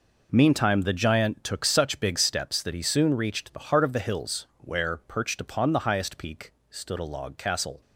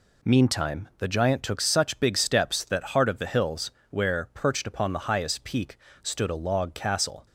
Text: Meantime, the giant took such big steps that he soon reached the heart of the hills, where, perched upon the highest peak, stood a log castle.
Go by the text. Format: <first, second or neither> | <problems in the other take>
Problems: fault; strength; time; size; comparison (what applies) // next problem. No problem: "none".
first | skips "he soon reached the"; at 2.8 s